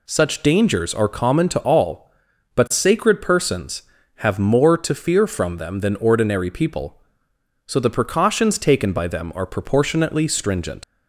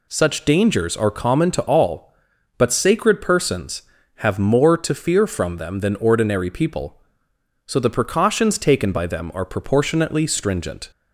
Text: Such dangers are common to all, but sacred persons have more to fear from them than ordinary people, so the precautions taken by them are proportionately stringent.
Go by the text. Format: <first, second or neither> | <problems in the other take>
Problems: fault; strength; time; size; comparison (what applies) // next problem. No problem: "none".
second | leaves "stringent" unfinished; at 10.8 s; 75 ms